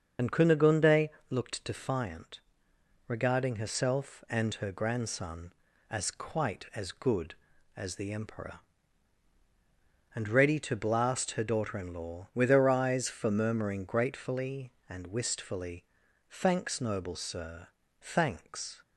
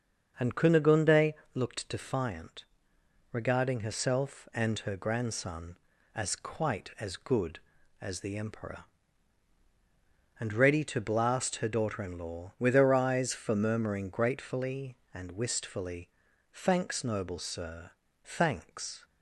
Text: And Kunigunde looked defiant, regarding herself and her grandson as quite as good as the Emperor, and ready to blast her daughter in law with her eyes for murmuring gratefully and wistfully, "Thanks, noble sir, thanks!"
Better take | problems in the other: second | loses the start of "And"; at 0.1 s; 55 ms // starts louder than the rest; until 1.4 s; 6.5 dB; also in the second // pauses between "Kunigunde" and "looked"; slight; at 1.0 s; 0.20 s long; slight in the second

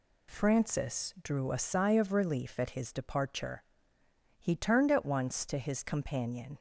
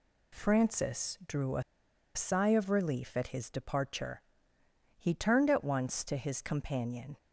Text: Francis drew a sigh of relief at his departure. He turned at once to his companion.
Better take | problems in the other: first | pauses between "a" and "sigh"; noticeable; at 1.6 s; 0.53 s long

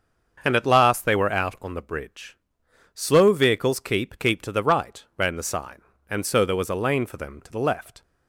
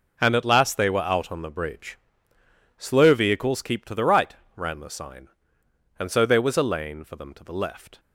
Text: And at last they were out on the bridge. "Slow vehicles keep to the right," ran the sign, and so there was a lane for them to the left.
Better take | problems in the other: second | starts louder than the rest; until 1.4 s; 6.5 dB // says "keep" twice; at 4.1 s

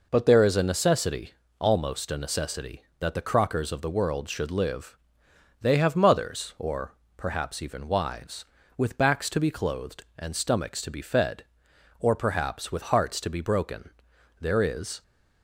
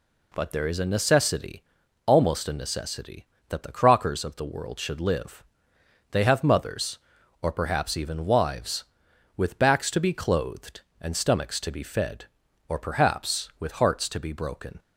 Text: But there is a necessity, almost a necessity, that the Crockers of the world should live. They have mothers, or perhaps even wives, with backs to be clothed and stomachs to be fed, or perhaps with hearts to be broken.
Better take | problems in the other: second | pauses between "or" and "perhaps"; slight; at 6.9 s; 0.22 s long // goes on to say "There is"; noticeable; from 14.4 s on; 0.62 s long

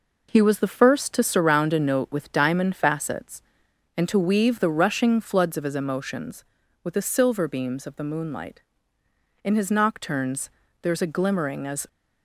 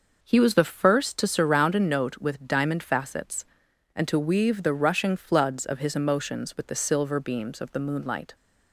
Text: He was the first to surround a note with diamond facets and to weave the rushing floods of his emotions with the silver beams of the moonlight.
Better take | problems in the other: second | goes on to say "In his nocturnes there is a glimmering as"; strong; from 9.4 s on; 2.4 s long

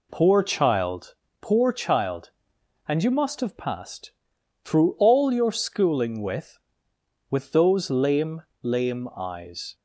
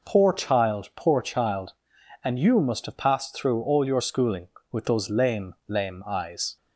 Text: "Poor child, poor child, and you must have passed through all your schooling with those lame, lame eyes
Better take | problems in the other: second | pauses between "passed" and "through"; noticeable; at 4.1 s; 0.53 s long // says "with" twice; at 7.2 s

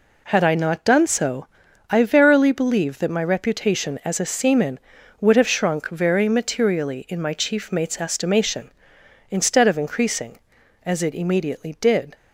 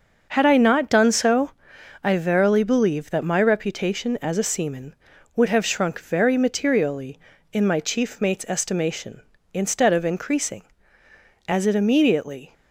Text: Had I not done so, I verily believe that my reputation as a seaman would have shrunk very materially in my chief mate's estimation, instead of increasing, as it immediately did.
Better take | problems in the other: first | starts louder than the rest; noticeable; until 1.2 s; 6 dB // stops before "did"; at 12.5 s

